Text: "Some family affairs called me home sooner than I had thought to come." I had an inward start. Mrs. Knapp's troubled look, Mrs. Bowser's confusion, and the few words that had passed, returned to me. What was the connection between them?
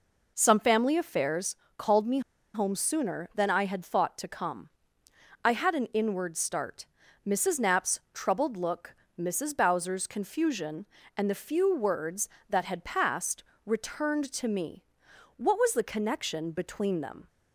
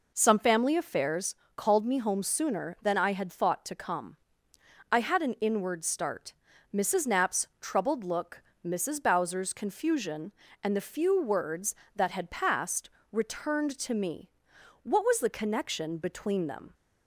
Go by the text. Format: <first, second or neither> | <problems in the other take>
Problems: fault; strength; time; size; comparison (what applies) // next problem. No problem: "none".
second | pauses between "affairs" and "called"; slight; at 1.5 s; 0.20 s long; slight in the second // pauses between "me" and "home"; slight; at 2.1 s; 0.34 s long